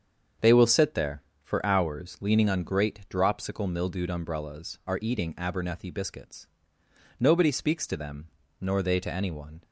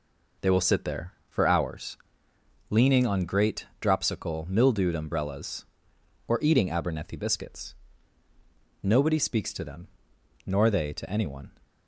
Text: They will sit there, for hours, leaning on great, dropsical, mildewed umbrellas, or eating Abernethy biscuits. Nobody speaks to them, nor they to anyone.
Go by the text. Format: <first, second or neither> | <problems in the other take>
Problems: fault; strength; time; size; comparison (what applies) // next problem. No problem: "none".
second | starts louder than the rest; until 1.6 s; 7 dB // says "are" for "or"; at 4.8 s